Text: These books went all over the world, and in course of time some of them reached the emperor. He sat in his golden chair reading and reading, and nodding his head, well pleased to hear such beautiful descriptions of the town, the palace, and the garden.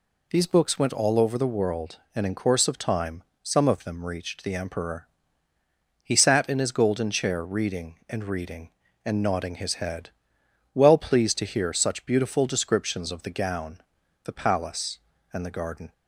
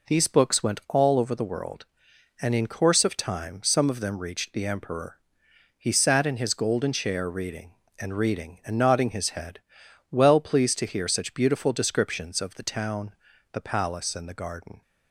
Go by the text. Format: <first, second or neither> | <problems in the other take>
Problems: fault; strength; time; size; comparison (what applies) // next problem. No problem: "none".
second | pauses between "time" and "some"; slight; at 3.2 s; 0.20 s long // says "gown" for "town"; at 13.3 s